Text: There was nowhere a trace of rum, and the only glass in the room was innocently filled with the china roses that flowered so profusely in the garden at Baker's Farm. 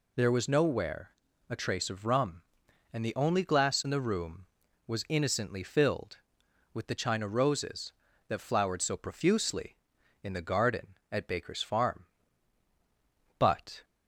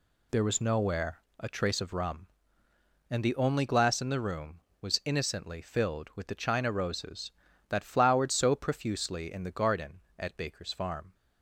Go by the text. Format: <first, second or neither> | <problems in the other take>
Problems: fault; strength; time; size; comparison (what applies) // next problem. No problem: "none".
second | pauses between "nowhere" and "a"; at 1.0 s; 0.40 s long; slight in the second // goes on to say "But"; slight; from 13.4 s on; 0.44 s long